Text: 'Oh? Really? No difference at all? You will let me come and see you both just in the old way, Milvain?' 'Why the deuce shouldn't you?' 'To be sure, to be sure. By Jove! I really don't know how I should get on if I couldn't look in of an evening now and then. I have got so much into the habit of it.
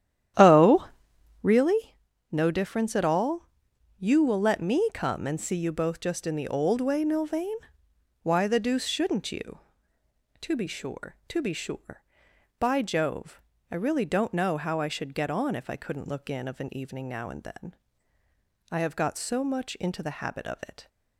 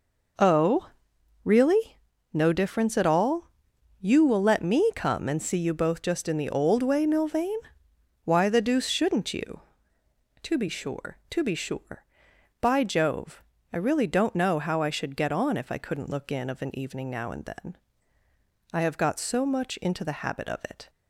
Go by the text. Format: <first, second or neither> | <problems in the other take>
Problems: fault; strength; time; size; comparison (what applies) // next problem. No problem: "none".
second | starts louder than the rest; strong; until 1.6 s; 10.5 dB